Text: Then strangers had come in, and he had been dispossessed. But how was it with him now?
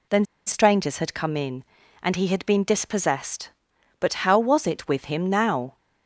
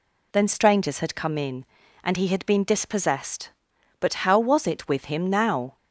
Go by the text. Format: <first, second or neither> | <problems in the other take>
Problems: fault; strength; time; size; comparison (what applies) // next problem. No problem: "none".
second | pauses between "Then" and "strangers"; slight; at 0.2 s; 0.22 s long